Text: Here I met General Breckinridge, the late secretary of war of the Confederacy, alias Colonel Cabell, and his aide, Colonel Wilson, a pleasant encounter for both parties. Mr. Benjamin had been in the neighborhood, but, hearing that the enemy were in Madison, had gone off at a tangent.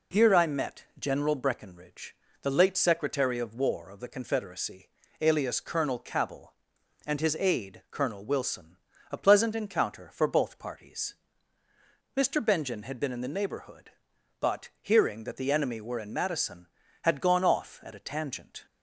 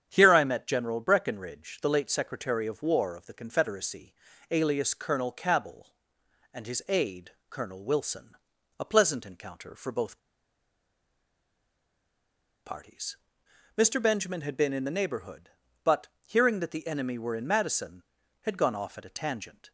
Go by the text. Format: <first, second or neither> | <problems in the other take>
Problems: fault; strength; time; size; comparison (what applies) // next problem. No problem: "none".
first | starts louder than the rest; strong; until 1.1 s; 8.5 dB // pauses between "both" and "parties"; strong; at 10.1 s; 2.4 s long